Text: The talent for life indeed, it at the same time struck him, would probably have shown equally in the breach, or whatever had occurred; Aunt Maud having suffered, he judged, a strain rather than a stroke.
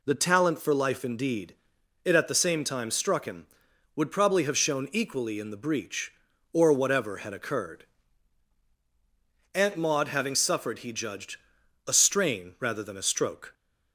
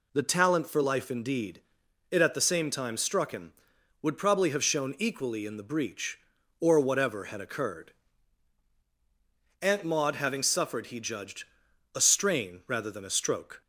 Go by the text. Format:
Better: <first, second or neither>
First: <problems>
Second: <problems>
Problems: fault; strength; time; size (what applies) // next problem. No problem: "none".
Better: neither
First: none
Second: none